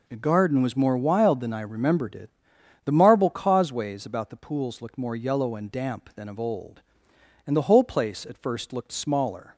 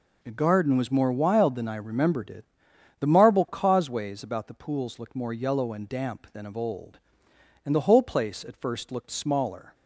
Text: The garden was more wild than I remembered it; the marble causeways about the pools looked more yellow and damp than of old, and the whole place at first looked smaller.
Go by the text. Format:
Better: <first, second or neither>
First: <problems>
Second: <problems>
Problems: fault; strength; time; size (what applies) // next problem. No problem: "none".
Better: neither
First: none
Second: none